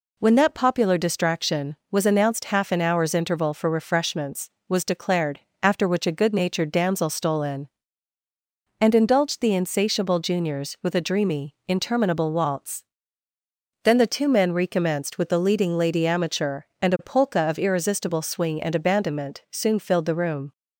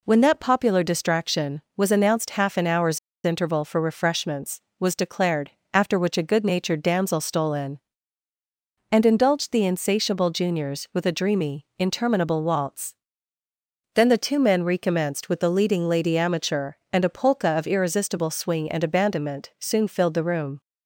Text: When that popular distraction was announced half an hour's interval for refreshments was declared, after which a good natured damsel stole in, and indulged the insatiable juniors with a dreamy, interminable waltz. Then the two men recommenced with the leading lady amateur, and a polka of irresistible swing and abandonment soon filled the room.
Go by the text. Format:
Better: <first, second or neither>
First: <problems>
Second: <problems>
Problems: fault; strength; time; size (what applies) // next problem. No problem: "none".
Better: first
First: none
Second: pauses between "hour's" and "interval"; slight; at 2.9 s; 0.25 s long